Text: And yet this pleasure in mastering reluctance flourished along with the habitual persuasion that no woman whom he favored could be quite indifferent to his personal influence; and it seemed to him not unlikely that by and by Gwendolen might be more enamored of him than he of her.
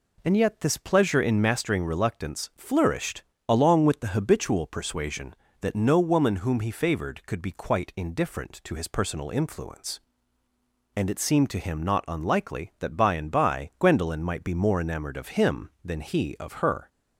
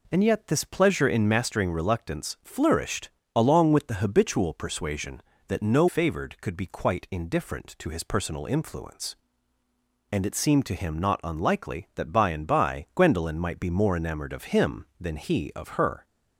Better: first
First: pauses between "flourished" and "along"; slight; at 3.2 s; 0.24 s long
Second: pauses between "flourished" and "along"; slight; at 3.0 s; 0.24 s long // skips "woman whom he"; at 5.8 s

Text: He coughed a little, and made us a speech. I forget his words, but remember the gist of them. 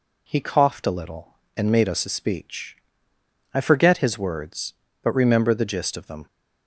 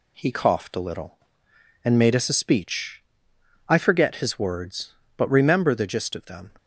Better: neither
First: none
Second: none

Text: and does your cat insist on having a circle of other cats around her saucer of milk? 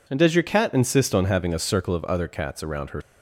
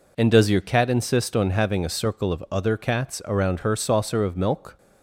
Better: second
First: stops before "saucer of milk"; at 3.0 s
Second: none

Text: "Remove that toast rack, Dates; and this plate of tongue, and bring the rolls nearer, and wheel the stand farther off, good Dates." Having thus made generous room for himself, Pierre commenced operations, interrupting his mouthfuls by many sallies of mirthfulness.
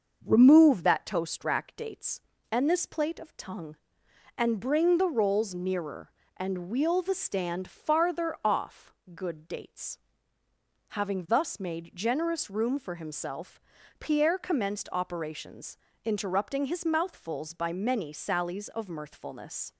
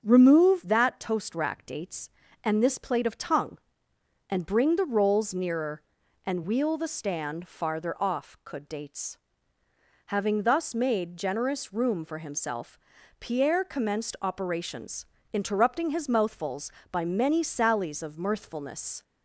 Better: first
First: starts louder than the rest; until 1.2 s; 6.5 dB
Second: starts louder than the rest; until 1.0 s; 6.5 dB // says "could" for "good"; at 8.4 s

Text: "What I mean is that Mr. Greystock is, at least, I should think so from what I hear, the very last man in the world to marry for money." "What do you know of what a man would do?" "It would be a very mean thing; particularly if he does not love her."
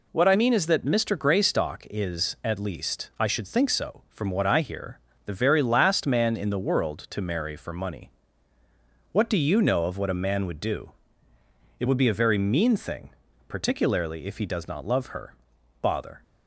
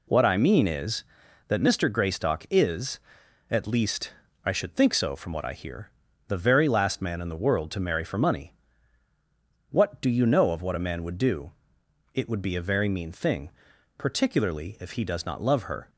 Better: second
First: goes on to say "Bother"; slight; from 15.8 s on; 0.42 s long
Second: none

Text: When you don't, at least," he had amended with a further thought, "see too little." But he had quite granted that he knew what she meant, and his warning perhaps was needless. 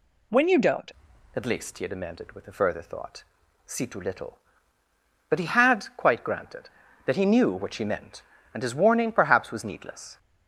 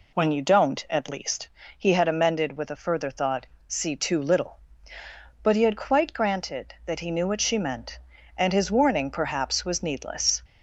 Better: second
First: changes voice at "at"; from 1.3 s on; 8.8 s long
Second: none

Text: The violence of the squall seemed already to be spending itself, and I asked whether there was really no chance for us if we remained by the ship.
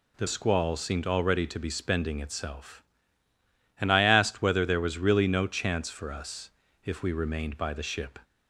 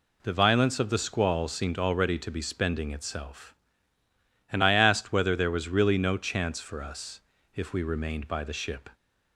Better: second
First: skips "violence of the"; at 0.2 s // pauses between "us" and "if"; slight; at 6.5 s; 0.34 s long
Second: pauses between "us" and "if"; slight; at 7.2 s; 0.34 s long

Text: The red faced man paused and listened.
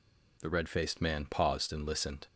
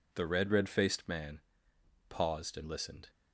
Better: first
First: none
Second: says "red" twice; at 0.5 s // pauses between "man" and "paused"; noticeable; at 1.3 s; 0.68 s long

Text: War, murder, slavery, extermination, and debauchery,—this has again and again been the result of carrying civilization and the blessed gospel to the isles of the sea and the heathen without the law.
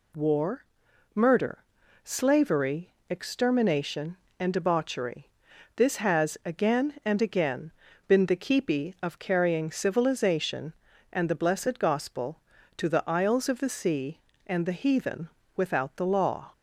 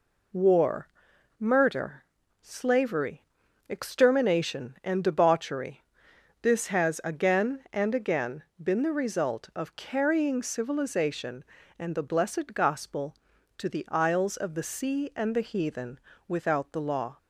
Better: second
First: pauses between "again" and "been"; slight; at 7.7 s; 0.34 s long // says "keepy" for "result"; at 8.3 s // pauses between "heathen" and "without"; slight; at 15.2 s; 0.26 s long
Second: pauses between "again" and "been"; slight; at 8.4 s; 0.18 s long // pauses between "heathen" and "without"; slight; at 15.9 s; 0.28 s long

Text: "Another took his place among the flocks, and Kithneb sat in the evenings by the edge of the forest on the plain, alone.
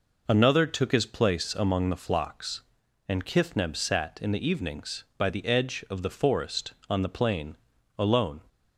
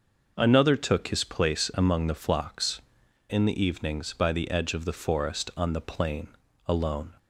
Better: first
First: none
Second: skips "and Kithneb sat"; at 3.0 s

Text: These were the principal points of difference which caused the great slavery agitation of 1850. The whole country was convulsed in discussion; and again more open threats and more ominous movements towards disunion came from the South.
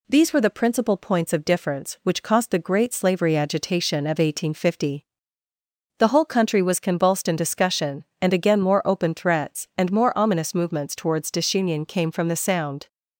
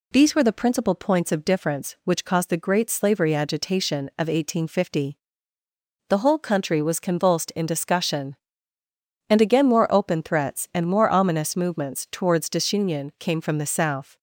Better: second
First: says "Sound" for "South"; at 12.3 s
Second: none

